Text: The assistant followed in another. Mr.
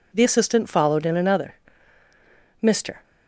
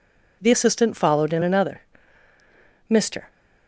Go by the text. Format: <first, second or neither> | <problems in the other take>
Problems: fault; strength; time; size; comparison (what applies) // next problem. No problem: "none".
neither | none